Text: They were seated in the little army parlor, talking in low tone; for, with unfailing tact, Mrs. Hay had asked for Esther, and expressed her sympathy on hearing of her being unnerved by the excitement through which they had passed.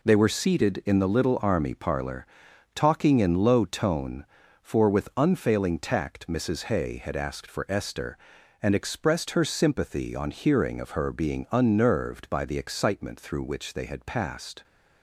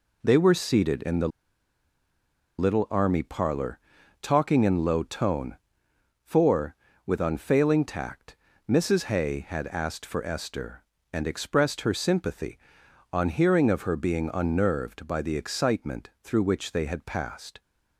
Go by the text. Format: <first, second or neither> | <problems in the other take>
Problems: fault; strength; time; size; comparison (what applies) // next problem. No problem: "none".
first | pauses between "the" and "little"; strong; at 1.2 s; 1.3 s long